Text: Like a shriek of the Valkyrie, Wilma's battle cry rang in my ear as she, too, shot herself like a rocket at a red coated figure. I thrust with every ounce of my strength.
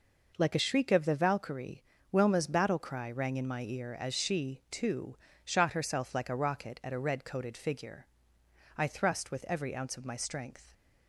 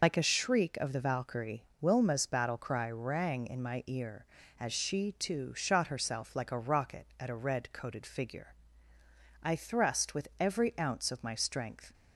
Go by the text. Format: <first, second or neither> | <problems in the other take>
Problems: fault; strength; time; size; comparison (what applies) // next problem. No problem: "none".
first | loses the start of "Like"; at 0.0 s; 55 ms